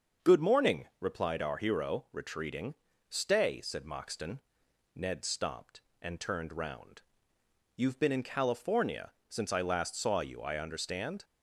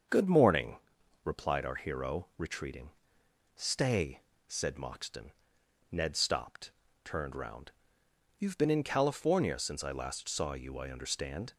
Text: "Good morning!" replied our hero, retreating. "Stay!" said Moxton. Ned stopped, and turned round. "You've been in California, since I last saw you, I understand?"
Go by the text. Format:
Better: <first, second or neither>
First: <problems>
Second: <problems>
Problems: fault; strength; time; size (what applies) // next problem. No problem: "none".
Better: first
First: starts louder than the rest; until 1.3 s; 6.5 dB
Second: starts louder than the rest; until 1.5 s; 6.5 dB // skips "and"; at 6.8 s